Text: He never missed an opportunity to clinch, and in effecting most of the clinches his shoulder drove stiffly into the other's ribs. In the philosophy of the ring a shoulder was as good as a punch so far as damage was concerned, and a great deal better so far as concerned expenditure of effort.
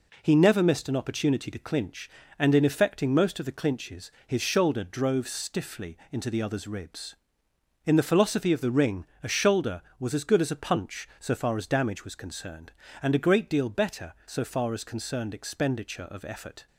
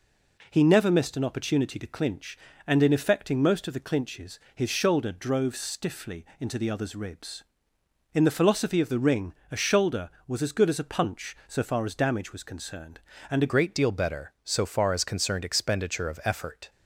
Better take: first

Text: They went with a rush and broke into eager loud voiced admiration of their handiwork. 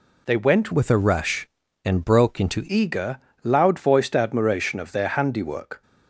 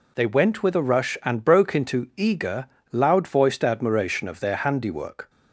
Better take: second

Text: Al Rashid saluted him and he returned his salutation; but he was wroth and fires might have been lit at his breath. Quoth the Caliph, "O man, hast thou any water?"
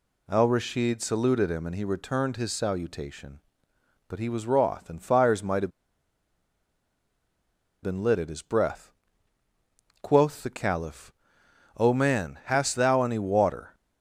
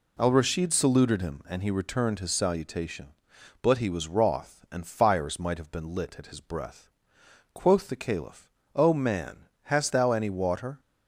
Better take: second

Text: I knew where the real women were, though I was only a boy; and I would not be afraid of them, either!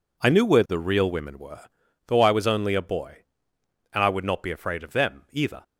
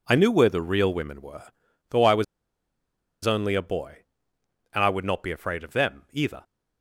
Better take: first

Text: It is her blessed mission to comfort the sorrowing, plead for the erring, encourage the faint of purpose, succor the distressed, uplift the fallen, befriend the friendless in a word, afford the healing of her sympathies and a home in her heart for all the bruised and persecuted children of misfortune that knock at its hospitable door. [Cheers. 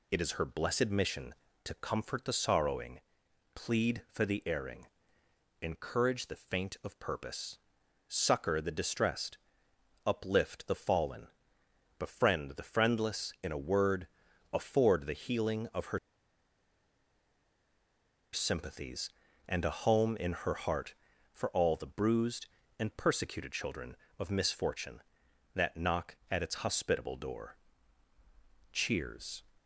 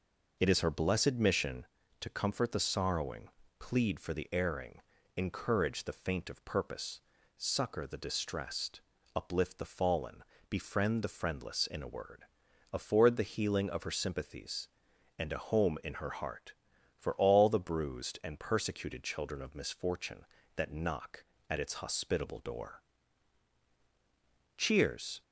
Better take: second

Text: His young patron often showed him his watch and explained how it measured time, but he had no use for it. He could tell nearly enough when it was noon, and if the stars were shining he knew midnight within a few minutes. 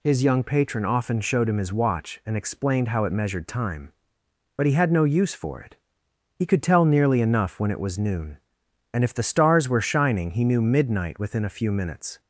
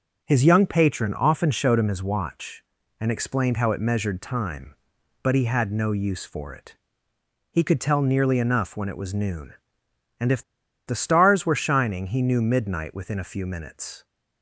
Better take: first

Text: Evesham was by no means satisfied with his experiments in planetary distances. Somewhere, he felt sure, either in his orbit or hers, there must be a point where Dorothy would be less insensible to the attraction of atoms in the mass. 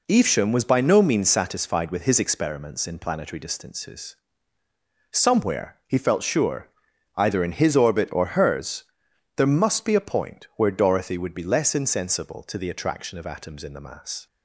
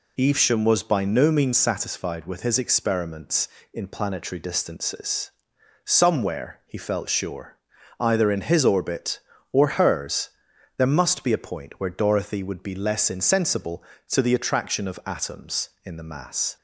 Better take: neither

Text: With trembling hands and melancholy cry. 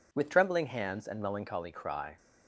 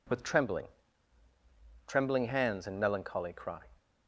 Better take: first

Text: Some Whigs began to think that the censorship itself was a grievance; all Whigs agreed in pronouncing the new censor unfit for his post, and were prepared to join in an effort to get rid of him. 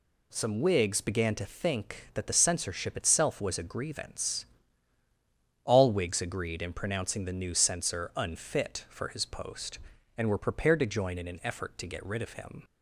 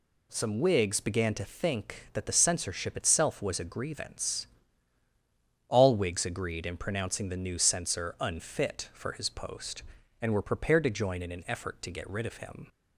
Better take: neither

